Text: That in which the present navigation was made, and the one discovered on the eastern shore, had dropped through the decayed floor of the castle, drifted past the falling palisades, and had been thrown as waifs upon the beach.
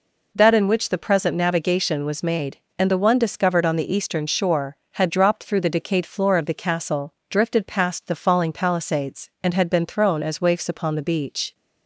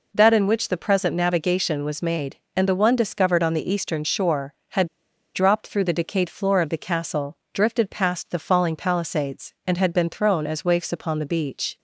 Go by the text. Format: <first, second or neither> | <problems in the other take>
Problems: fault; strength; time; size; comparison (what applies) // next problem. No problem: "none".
first | pauses between "had" and "dropped"; noticeable; at 4.8 s; 0.47 s long